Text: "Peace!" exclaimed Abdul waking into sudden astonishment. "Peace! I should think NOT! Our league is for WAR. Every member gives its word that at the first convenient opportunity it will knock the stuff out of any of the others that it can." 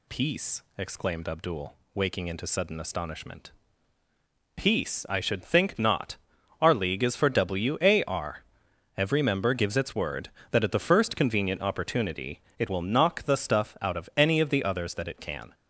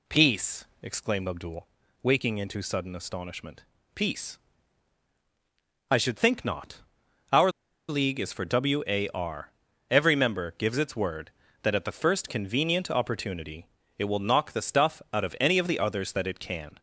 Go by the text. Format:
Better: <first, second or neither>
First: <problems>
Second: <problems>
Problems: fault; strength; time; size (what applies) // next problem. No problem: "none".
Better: first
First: pauses between "Abdul" and "waking"; slight; at 1.7 s; 0.20 s long // pauses between "opportunity" and "it"; slight; at 12.3 s; 0.18 s long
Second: pauses between "Abdul" and "waking"; at 1.6 s; 0.38 s long // pauses between "Our" and "league"; at 7.4 s; 0.38 s long // pauses between "opportunity" and "it"; slight; at 13.6 s; 0.30 s long